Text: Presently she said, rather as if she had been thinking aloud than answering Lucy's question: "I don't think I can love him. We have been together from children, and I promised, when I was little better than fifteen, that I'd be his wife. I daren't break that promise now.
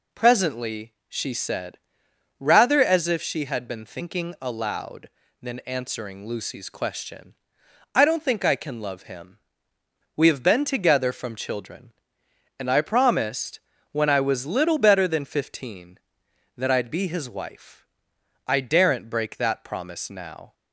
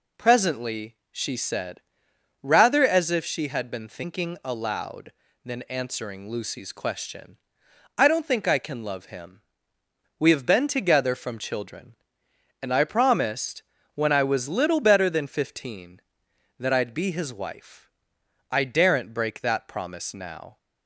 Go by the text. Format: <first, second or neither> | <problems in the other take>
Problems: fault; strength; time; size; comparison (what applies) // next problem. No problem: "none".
neither | none